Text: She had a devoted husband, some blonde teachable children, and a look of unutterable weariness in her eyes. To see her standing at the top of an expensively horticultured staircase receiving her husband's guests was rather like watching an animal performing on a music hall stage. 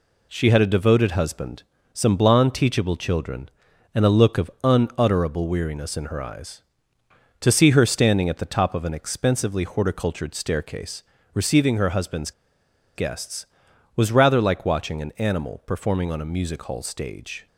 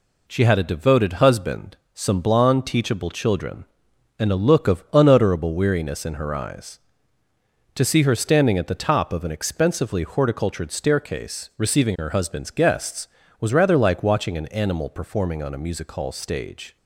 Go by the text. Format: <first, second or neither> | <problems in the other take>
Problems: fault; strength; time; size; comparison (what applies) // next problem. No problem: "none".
second | pauses between "staircase" and "receiving"; slight; at 11.0 s; 0.30 s long // pauses between "husband's" and "guests"; noticeable; at 12.3 s; 0.64 s long